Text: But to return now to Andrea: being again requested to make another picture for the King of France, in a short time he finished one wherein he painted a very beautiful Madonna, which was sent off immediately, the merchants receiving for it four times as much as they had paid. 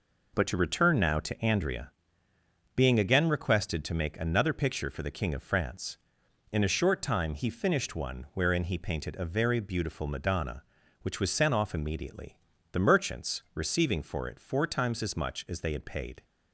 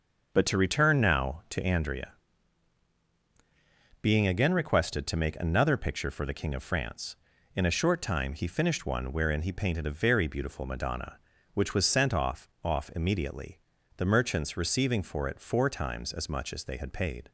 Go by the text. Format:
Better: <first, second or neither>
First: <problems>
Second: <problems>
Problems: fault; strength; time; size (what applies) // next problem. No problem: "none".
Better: first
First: none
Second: starts louder than the rest; noticeable; until 1.3 s; 6 dB // says "off" twice; at 12.6 s